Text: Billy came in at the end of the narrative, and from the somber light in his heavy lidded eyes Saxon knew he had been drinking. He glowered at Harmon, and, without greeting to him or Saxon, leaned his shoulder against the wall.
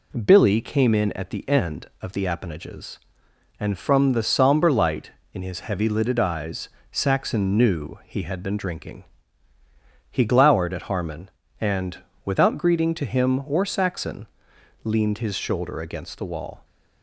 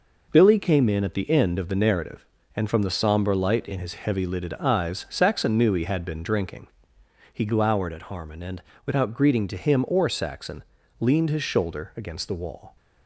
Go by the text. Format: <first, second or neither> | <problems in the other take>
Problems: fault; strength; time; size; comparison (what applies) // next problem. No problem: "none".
second | says "appanages" for "narrative"; at 2.2 s // pauses between "eyes" and "Saxon"; slight; at 6.6 s; 0.24 s long